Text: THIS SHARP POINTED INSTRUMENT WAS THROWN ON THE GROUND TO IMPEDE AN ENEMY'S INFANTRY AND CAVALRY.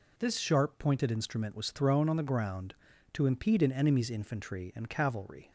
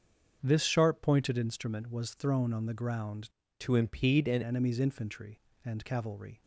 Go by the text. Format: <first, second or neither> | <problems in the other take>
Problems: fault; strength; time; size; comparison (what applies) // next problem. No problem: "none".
first | starts louder than the rest; until 1.4 s; 6.5 dB // changes voice from "TO" to "AN"; from 3.5 to 4.4 s; 0.9 s long